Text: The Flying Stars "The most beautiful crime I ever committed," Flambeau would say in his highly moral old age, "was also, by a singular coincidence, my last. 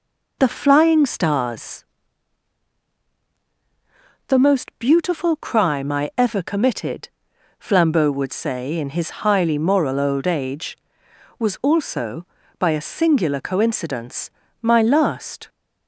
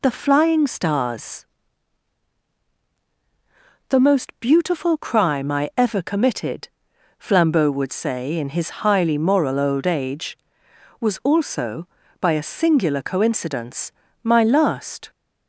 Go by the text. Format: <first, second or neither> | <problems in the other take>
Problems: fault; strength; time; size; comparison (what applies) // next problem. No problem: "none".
second | starts louder than the rest; noticeable; until 1.4 s; 4.5 dB // pauses between "Stars" and "The"; strong; at 1.8 s; 2.4 s long; strong in the second